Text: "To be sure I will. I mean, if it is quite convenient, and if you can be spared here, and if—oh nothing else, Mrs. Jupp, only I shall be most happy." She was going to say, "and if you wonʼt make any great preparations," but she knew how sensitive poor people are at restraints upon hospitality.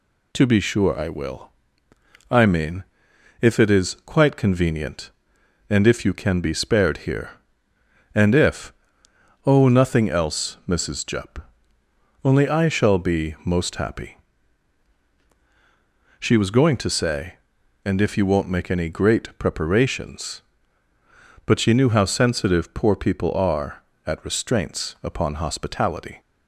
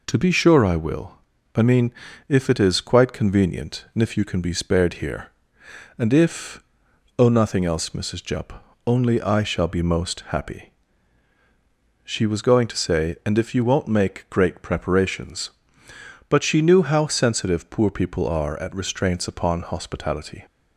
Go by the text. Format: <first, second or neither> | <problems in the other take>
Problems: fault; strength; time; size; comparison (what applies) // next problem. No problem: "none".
first | skips "any"; at 14.2 s